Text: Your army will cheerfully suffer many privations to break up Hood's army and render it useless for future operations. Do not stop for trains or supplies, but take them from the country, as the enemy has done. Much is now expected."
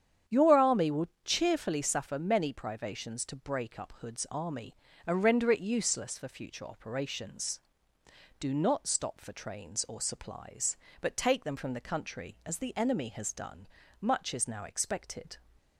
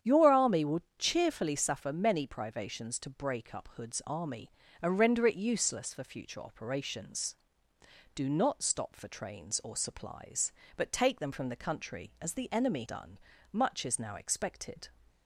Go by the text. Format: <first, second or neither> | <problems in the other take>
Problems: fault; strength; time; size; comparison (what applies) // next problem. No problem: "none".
first | starts louder than the rest; strong; until 1.2 s; 9 dB; strong in the first // pauses between "will" and "cheerfully"; slight; at 0.8 s; 0.18 s long; slight in the first // skips "has"; at 12.8 s